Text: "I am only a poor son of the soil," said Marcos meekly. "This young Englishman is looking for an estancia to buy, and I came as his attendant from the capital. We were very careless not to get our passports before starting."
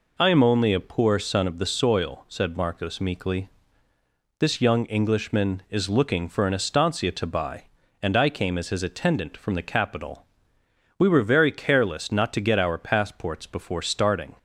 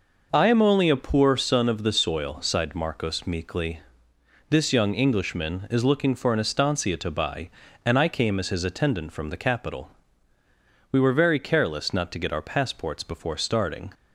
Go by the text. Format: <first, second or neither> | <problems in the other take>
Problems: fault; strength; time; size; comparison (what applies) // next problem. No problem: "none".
first | says "sighed" for "said"; at 2.4 s